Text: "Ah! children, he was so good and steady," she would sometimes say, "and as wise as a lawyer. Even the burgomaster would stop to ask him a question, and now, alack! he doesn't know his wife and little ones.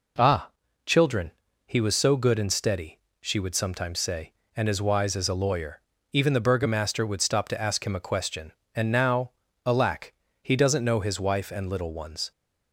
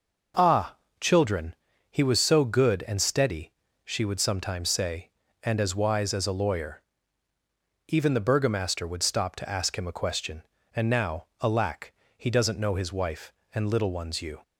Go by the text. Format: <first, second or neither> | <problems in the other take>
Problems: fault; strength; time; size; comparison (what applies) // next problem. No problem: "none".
first | goes on to say "You"; slight; from 14.2 s on; 0.20 s long